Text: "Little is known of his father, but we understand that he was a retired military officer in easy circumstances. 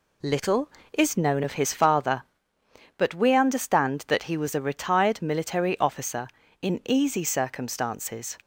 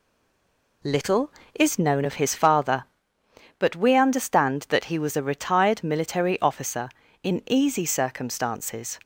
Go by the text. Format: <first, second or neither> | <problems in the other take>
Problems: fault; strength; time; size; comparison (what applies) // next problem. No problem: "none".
first | stays silent before the first word; slight; until 0.8 s; 0.8 s long